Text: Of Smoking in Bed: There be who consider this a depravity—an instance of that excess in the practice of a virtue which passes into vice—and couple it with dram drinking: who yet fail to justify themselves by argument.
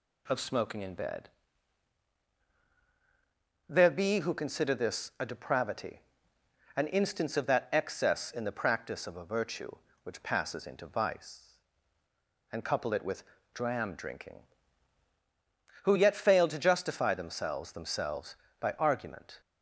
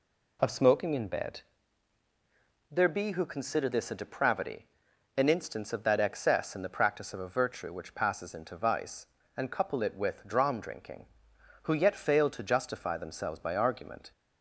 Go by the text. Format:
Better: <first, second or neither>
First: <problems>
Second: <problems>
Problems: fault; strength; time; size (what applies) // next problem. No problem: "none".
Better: second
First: pauses between "with" and "dram"; slight; at 13.2 s; 0.32 s long // says "themselves" twice; at 17.7 s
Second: none